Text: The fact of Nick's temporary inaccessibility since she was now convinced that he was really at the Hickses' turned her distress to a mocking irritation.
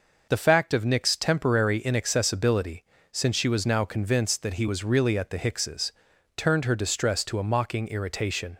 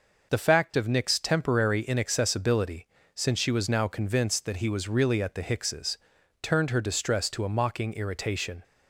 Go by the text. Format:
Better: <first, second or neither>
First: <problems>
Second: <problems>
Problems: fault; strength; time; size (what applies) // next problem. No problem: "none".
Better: neither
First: pauses between "inaccessibility" and "since"; slight; at 2.8 s; 0.28 s long // pauses between "Hickses" and "turned"; noticeable; at 5.9 s; 0.46 s long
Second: pauses between "inaccessibility" and "since"; slight; at 2.8 s; 0.28 s long // pauses between "Hickses" and "turned"; noticeable; at 5.9 s; 0.46 s long